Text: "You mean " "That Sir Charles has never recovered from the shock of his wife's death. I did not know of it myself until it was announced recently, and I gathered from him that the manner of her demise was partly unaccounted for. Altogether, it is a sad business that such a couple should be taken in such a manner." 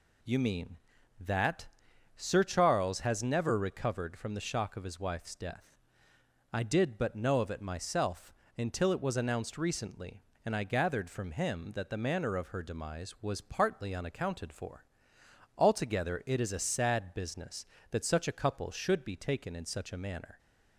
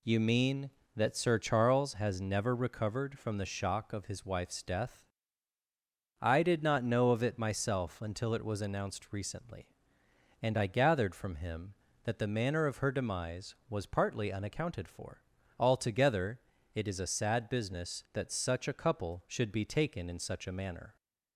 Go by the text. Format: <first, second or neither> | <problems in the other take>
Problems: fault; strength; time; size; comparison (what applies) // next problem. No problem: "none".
second | pauses between "That" and "Sir"; noticeable; at 1.6 s; 0.50 s long // says "but" for "not"; at 6.9 s // pauses between "myself" and "until"; slight; at 8.3 s; 0.24 s long